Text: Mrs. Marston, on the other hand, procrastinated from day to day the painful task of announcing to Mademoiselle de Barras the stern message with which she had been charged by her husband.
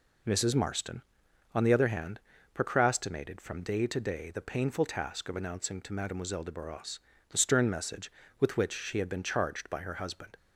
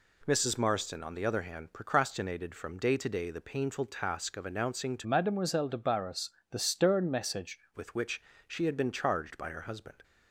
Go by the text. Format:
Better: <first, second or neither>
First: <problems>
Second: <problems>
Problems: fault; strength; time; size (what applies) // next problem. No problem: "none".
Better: first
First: pauses between "Barras" and "the"; slight; at 6.9 s; 0.30 s long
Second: changes voice from "Mademoiselle" to "message"; from 5.0 to 7.5 s; 2.5 s long // pauses between "Barras" and "the"; slight; at 6.2 s; 0.22 s long // pauses between "which" and "she"; slight; at 8.2 s; 0.24 s long